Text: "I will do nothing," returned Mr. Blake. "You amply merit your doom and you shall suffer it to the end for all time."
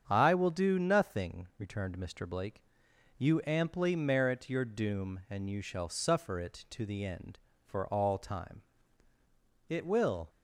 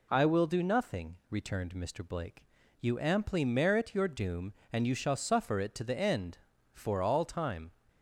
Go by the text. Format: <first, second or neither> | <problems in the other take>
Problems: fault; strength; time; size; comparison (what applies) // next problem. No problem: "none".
second | starts louder than the rest; strong; until 1.0 s; 7.5 dB // goes on to say "It will"; noticeable; from 9.6 s on; 0.62 s long